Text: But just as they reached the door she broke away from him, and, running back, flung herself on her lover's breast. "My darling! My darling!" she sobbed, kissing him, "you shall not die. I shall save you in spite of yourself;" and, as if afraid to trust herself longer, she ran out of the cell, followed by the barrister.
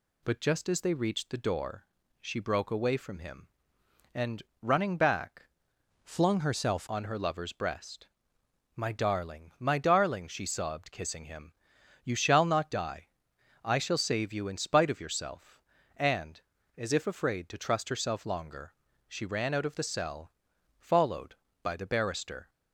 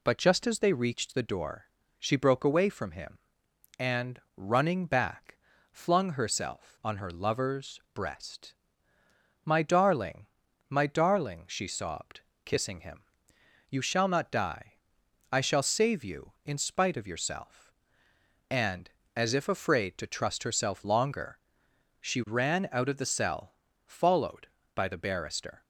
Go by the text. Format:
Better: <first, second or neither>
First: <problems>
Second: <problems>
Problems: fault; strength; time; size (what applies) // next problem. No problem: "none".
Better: second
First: pauses between "door" and "she"; slight; at 1.8 s; 0.34 s long // changes voice from "flung" to "herself"; from 6.0 to 6.8 s; 0.8 s long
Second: pauses between "door" and "she"; at 1.6 s; 0.38 s long